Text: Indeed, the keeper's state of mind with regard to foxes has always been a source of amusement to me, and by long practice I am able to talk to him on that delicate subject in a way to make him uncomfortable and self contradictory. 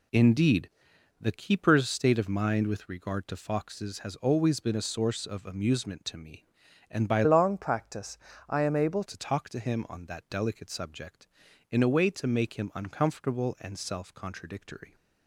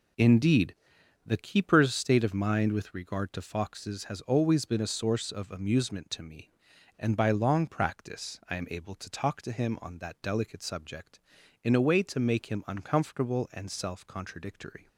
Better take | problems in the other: second | changes voice from "long" to "able"; from 7.2 to 9.0 s; 1.8 s long // pauses between "practice" and "I"; slight; at 8.1 s; 0.32 s long

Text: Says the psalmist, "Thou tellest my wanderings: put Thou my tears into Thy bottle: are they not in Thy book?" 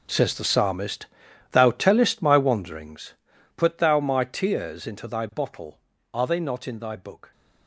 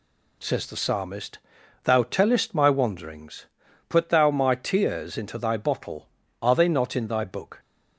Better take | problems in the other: second | gets quieter; strong; throughout; 15 dB

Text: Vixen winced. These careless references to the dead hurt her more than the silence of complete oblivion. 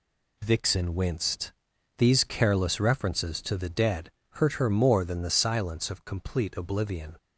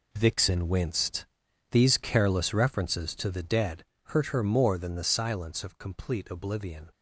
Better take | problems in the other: first | gets quieter; strong; throughout; 11 dB // pauses between "dead" and "hurt"; slight; at 3.8 s; 0.22 s long; slight in the first

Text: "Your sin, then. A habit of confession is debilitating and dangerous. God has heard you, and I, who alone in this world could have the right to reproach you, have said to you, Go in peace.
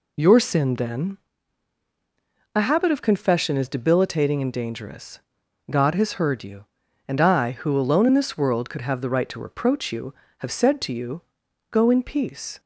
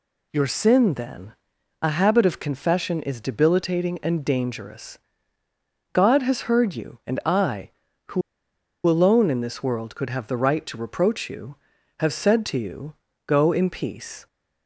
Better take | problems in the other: first | pauses between "who" and "alone"; noticeable; at 8.2 s; 0.65 s long

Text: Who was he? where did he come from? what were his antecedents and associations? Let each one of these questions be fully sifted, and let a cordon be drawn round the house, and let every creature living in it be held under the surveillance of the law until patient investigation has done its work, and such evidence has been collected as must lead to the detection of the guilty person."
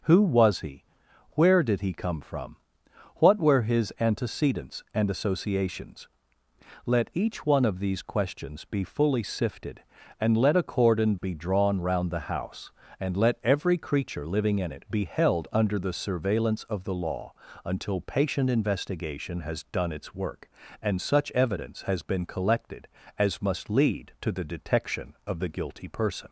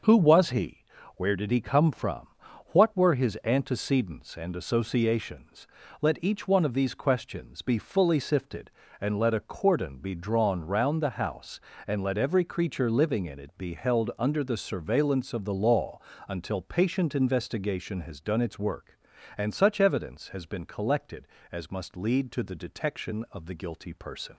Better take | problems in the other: neither | starts louder than the rest; the same in both // pauses between "law" and "until"; slight; the same in both

